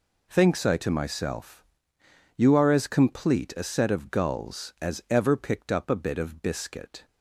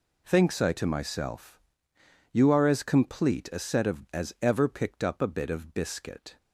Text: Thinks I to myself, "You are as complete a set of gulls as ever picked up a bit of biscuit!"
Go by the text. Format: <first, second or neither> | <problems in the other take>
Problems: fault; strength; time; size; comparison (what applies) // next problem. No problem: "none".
first | skips "gulls"; at 4.0 s